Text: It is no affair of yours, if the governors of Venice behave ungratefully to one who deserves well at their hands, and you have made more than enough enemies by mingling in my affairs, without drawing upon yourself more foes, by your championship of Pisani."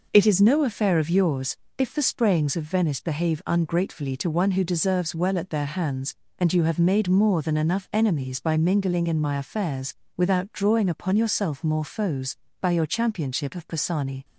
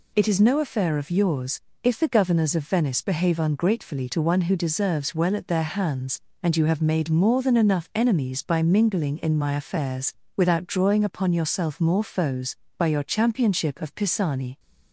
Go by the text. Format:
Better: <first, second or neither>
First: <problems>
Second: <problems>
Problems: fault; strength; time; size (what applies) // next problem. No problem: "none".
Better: second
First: says "sprayings" for "governors"; at 2.0 s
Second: none